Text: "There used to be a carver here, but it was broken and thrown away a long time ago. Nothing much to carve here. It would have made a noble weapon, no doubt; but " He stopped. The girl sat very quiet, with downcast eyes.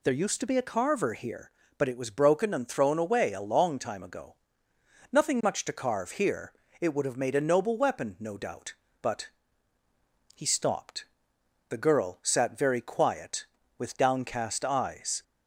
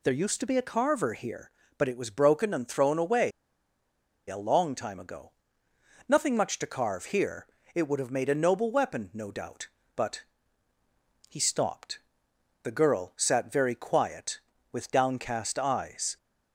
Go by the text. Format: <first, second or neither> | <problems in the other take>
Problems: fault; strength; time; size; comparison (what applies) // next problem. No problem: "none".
first | pauses between "away" and "a"; noticeable; at 3.3 s; 0.97 s long